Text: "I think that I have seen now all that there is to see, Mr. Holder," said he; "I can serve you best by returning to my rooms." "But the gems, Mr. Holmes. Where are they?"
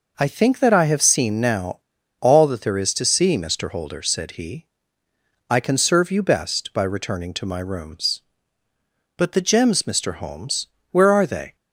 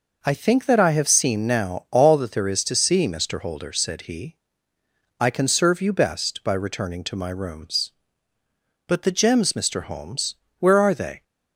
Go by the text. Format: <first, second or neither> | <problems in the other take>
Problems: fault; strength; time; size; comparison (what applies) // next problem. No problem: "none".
second | pauses between "now" and "all"; at 1.7 s; 0.40 s long